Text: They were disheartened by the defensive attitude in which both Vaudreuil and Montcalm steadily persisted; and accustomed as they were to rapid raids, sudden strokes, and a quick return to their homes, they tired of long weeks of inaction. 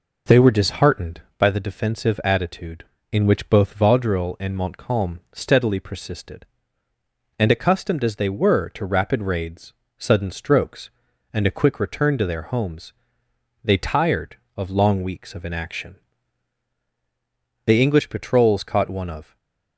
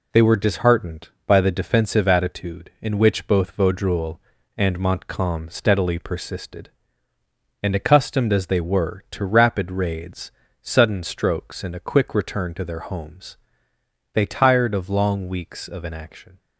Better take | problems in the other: second | goes on to say "The English patrols caught one of"; strong; from 17.6 s on; 1.7 s long // stays silent after the last word; slight; from 19.2 s on; 0.5 s long

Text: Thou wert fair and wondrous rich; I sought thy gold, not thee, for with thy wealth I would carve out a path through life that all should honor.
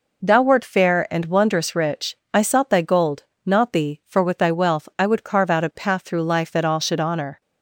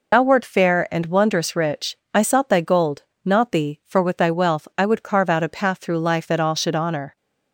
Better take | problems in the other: first | loses the start of "Thou"; at 0.1 s; 100 ms

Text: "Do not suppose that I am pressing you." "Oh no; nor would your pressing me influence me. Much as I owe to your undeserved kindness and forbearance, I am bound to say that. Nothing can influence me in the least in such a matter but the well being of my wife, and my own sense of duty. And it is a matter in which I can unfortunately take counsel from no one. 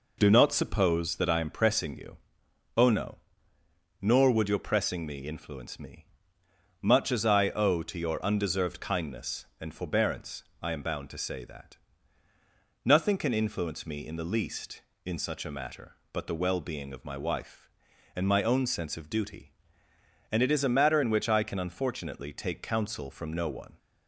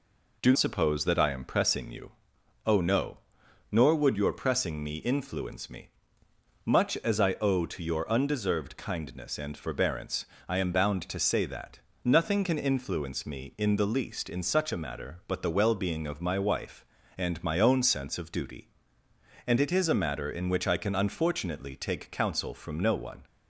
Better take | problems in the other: first | skips "not"; at 0.5 s

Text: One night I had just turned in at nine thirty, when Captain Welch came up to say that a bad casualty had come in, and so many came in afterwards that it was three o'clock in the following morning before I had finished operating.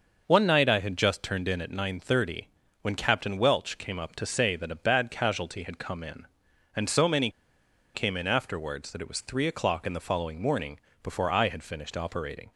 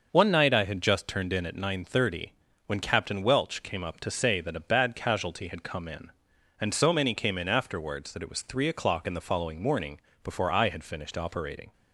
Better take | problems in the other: second | pauses between "many" and "came"; noticeable; at 7.2 s; 0.65 s long // pauses between "morning" and "before"; slight; at 10.7 s; 0.22 s long; slight in the second

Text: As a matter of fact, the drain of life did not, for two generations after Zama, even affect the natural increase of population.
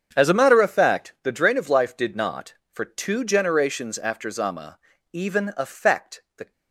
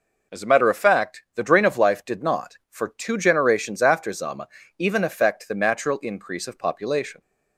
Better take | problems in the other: second | starts louder than the rest; strong; until 1.1 s; 7.5 dB // stops before "natural increase of population"; at 6.5 s

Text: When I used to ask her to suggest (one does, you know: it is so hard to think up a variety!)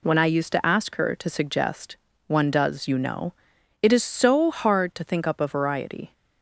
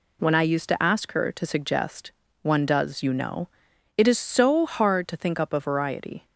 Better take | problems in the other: neither | none

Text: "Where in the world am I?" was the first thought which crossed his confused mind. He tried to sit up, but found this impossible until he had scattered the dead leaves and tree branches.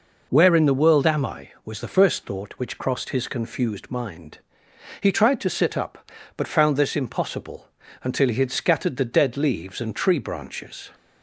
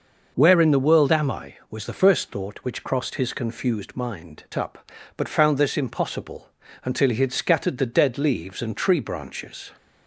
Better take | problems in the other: first | skips "He tried to sit"; at 4.5 s // pauses between "impossible" and "until"; slight; at 6.5 s; 0.34 s long; slight in the first

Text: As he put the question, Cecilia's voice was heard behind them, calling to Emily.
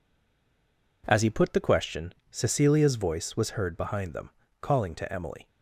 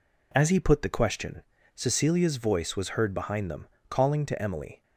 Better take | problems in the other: second | stays silent before the first word; until 1.0 s; 1.0 s long

